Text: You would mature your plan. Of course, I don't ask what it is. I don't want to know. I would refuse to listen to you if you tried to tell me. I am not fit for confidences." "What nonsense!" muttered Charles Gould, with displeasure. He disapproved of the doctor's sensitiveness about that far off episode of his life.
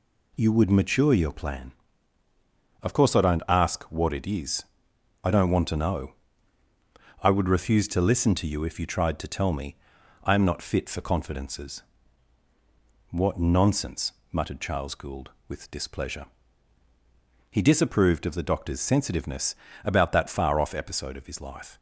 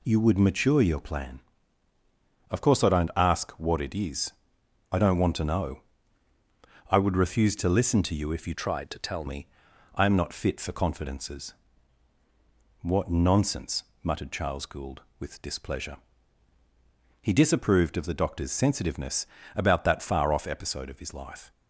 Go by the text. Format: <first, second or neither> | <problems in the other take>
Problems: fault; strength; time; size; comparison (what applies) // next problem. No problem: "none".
first | changes voice from "tried" to "tell"; from 8.5 to 9.2 s; 0.7 s long // pauses between "sensitiveness" and "about"; slight; at 19.2 s; 0.30 s long; slight in the first